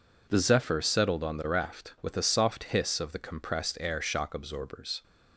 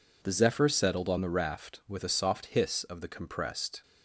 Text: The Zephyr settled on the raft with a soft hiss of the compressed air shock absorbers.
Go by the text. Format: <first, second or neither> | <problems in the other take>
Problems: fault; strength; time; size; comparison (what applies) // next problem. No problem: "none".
first | stops before "air shock absorbers"; at 3.8 s